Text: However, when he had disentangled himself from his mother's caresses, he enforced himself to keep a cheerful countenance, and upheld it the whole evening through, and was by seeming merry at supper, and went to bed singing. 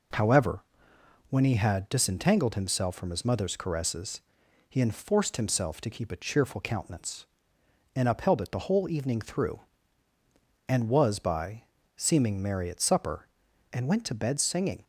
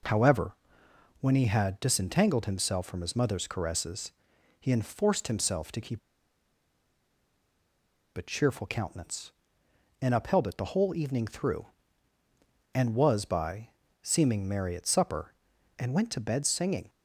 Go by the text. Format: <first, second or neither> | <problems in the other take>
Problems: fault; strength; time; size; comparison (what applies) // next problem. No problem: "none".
first | pauses between "keep" and "a"; strong; at 5.9 s; 2.1 s long // pauses between "by" and "seeming"; slight; at 13.6 s; 0.32 s long; slight in the first